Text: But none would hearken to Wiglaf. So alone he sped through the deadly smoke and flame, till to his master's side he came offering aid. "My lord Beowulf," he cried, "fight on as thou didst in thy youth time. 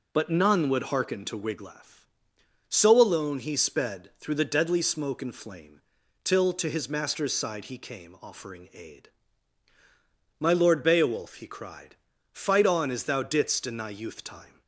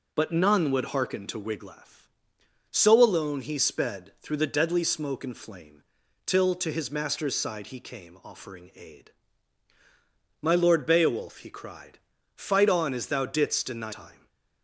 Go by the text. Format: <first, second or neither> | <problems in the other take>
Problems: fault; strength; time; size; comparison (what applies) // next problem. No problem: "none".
first | skips "youth"; at 13.9 s // stays silent after the last word; slight; from 14.1 s on; 0.5 s long